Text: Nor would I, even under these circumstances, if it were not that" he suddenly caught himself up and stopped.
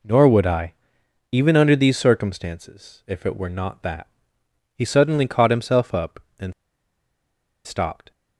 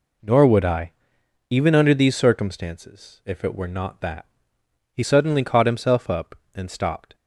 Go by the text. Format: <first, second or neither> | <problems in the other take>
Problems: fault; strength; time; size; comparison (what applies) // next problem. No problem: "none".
second | pauses between "that" and "he"; noticeable; at 4.0 s; 0.70 s long; noticeable in the second // pauses between "and" and "stopped"; at 6.5 s; 1.1 s long